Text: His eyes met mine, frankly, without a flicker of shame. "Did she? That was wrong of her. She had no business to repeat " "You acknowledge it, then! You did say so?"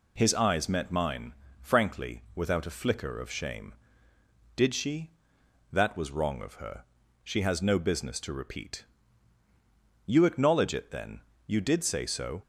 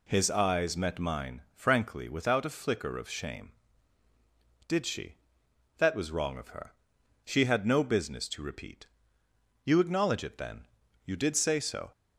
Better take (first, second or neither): second